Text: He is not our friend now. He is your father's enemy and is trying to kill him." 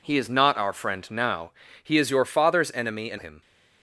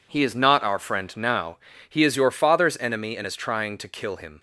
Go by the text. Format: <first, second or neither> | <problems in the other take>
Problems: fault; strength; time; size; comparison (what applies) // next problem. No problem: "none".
second | skips "is trying to kill"; at 3.1 s